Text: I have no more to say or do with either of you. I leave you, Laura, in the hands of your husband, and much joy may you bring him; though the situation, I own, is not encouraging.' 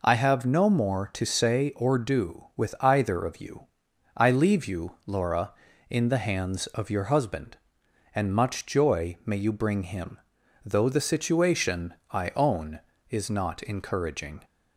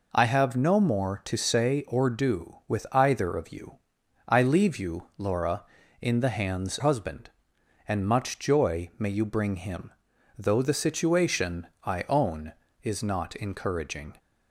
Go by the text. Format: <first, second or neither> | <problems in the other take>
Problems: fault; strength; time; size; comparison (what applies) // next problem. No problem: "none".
first | skips "of your"; at 6.7 s